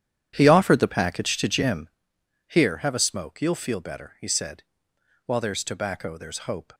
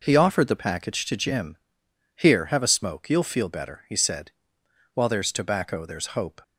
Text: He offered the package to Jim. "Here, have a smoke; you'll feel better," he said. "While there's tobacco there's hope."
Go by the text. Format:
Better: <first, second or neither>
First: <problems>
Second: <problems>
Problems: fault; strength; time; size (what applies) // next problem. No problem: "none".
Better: second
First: starts louder than the rest; strong; until 2.0 s; 10 dB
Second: none